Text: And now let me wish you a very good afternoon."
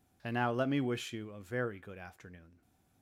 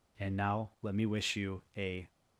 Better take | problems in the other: first | stops before "very good afternoon"; at 2.0 s

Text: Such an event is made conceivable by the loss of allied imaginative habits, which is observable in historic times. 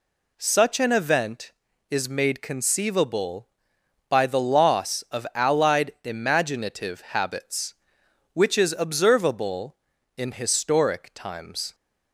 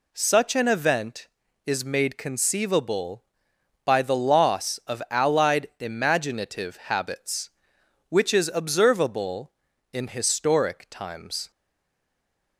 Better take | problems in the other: first | stays silent after the last word; from 11.5 s on; 1.0 s long

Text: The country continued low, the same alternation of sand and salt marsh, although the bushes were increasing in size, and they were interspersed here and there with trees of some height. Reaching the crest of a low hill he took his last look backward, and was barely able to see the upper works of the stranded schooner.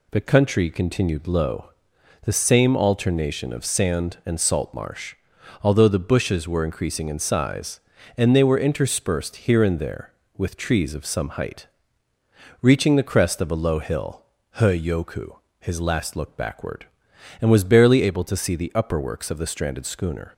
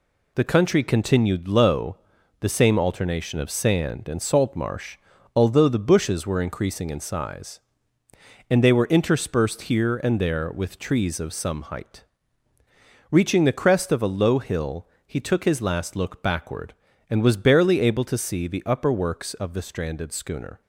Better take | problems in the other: second | pauses between "hill" and "he"; slight; at 14.2 s; 0.34 s long; slight in the second // says "yoku" for "took"; at 14.8 s

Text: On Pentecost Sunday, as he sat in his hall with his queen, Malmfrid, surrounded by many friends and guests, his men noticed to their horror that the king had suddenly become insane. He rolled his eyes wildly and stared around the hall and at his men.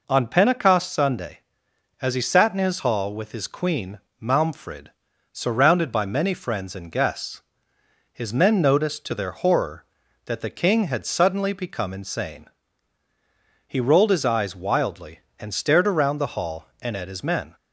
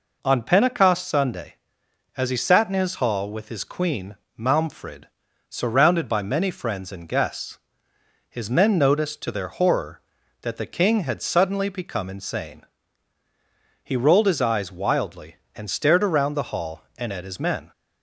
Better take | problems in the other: neither | none

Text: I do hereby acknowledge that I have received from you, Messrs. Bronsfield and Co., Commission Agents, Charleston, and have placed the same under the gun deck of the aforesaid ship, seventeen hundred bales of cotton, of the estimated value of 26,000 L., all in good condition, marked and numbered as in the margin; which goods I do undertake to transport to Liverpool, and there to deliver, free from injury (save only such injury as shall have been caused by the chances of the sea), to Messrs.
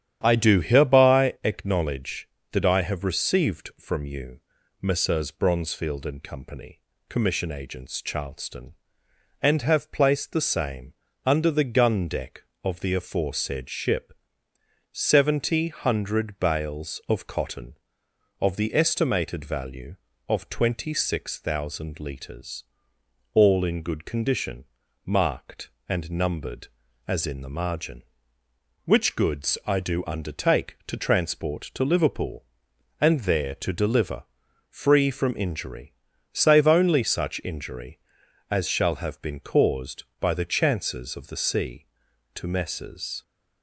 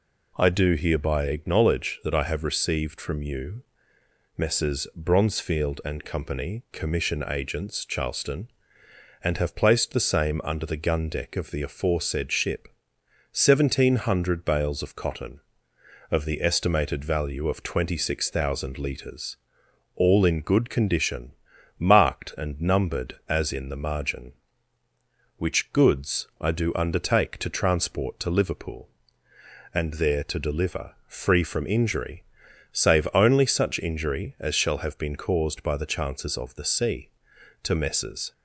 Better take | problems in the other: second | starts louder than the rest; strong; until 1.2 s; 11 dB // pauses between "same" and "under"; slight; at 10.9 s; 0.34 s long // says "seventy" for "seventeen"; at 14.9 s

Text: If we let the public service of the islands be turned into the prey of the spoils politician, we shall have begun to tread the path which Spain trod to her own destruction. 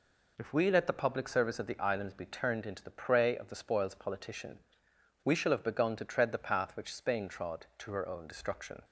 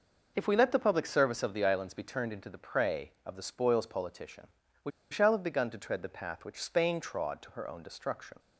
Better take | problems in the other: first | pauses between "we" and "shall"; slight; at 4.9 s; 0.20 s long

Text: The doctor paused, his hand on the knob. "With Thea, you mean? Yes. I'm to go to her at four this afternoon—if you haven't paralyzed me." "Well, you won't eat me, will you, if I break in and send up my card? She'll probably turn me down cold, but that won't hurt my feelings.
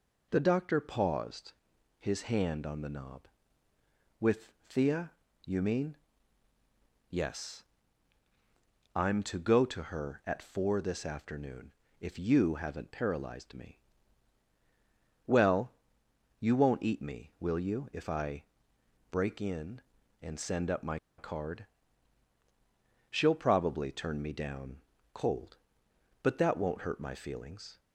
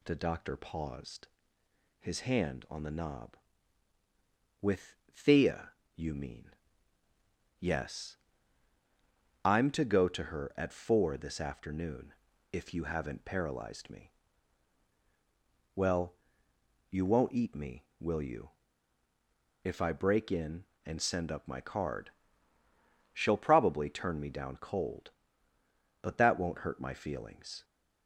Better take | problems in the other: second | pauses between "With" and "Thea"; slight; at 4.5 s; 0.16 s long; slight in the second // pauses between "I" and "break"; noticeable; at 18.4 s; 0.66 s long // pauses between "my" and "card"; slight; at 20.9 s; 0.19 s long // pauses between "down" and "cold"; slight; at 24.7 s; 0.32 s long

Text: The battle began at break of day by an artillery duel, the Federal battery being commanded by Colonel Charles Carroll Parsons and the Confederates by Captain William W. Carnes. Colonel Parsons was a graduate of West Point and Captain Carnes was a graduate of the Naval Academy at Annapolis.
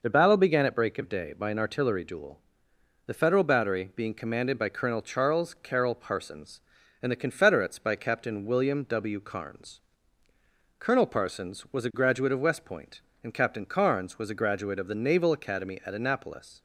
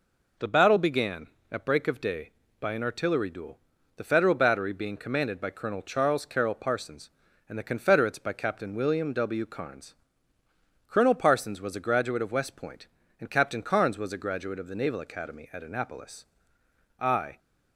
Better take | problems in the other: first | goes on to say "I"; slight; from 17.0 s on; 0.38 s long

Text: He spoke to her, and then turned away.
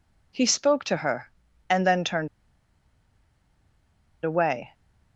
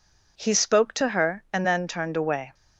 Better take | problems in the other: second | pauses between "turned" and "away"; strong; at 2.2 s; 1.9 s long

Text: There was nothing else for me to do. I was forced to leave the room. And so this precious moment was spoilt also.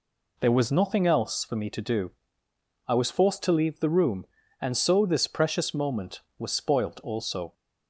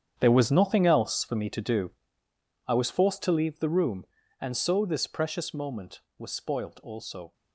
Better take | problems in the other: first | gets quieter; strong; throughout; 14 dB

